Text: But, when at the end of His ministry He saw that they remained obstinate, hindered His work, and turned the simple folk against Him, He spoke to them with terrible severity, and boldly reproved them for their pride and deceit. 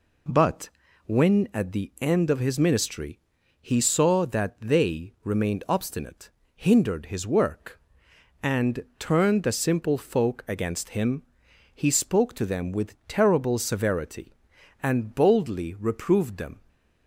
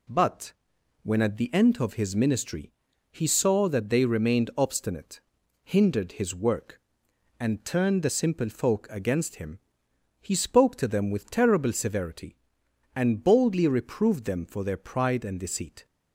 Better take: second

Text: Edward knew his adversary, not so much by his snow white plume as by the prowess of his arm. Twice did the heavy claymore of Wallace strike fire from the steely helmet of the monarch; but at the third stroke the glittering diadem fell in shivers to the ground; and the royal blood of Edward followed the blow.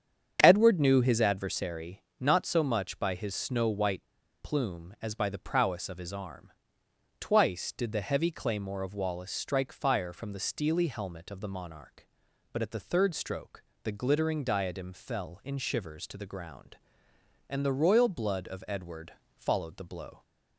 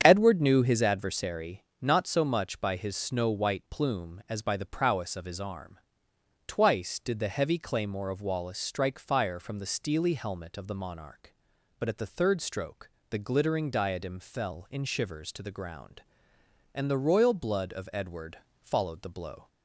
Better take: second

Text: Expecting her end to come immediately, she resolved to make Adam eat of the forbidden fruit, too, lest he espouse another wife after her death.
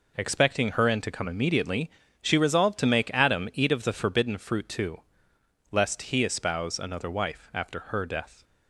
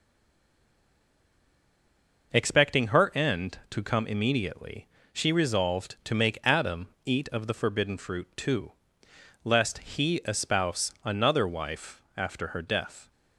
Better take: first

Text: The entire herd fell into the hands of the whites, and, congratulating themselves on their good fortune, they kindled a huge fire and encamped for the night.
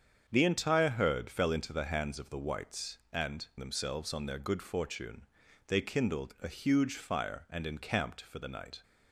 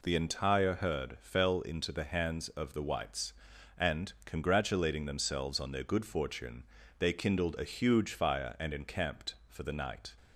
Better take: second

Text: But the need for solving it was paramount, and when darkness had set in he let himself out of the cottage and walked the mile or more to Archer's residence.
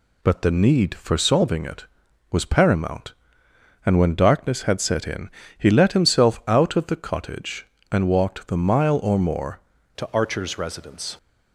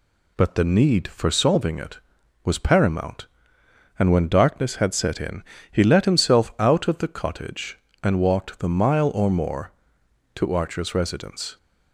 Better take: second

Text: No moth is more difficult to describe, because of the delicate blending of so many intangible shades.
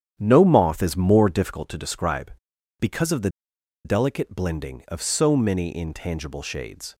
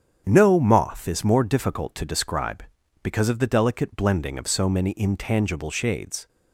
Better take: second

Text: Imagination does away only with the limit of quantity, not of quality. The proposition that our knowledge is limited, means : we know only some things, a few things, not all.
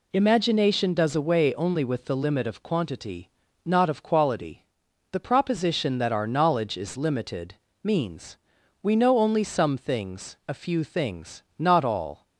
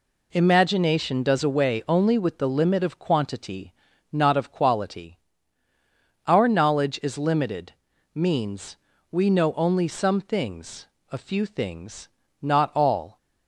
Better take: first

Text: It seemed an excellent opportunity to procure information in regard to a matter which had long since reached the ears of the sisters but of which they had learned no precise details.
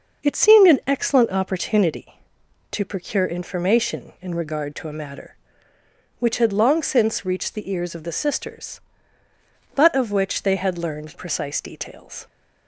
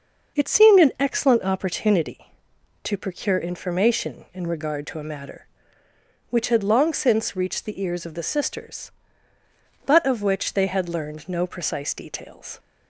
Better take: second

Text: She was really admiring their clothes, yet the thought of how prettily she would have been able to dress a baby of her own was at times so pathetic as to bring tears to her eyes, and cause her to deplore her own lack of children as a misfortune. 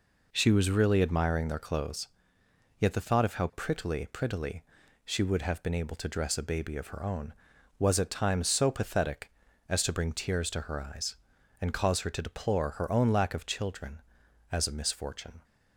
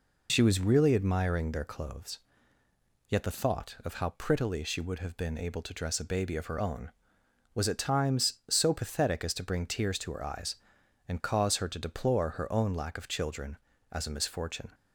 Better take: second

